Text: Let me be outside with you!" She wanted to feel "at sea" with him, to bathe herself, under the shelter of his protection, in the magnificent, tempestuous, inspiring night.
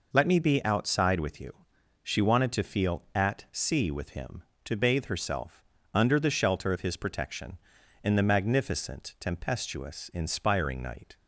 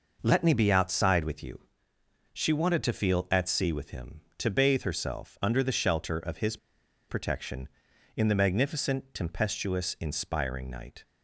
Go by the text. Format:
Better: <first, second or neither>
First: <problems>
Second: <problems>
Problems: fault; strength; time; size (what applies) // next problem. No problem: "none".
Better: first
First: none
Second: pauses between "his" and "protection"; noticeable; at 6.5 s; 0.53 s long